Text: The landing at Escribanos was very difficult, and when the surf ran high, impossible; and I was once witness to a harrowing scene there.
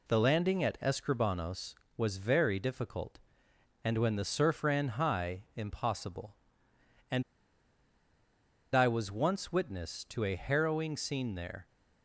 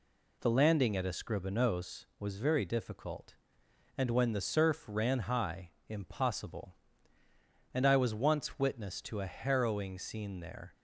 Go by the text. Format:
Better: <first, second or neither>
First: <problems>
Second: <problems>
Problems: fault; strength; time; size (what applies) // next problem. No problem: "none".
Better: second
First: pauses between "and" and "I"; strong; at 7.2 s; 1.5 s long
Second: none